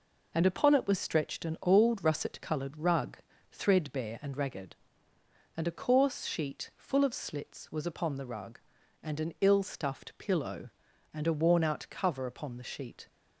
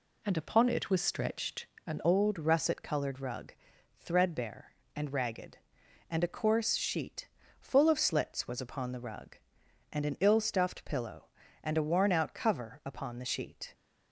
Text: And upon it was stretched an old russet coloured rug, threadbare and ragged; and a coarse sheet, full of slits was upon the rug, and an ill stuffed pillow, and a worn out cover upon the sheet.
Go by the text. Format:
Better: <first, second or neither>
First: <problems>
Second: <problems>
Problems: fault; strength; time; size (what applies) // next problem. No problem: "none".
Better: first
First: none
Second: pauses between "stretched" and "an"; slight; at 1.6 s; 0.20 s long // changes voice at "old"; from 2.0 s on; 11.7 s long